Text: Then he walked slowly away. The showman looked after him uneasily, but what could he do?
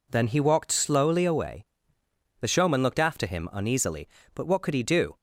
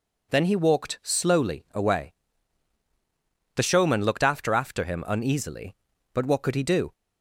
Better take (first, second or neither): first